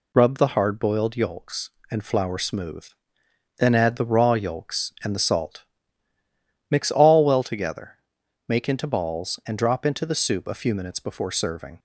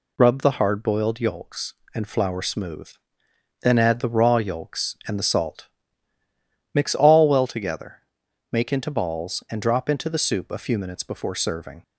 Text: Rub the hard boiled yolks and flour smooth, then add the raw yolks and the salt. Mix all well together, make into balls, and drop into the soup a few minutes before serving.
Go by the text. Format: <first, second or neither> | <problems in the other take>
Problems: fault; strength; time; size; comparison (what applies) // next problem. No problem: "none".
neither | none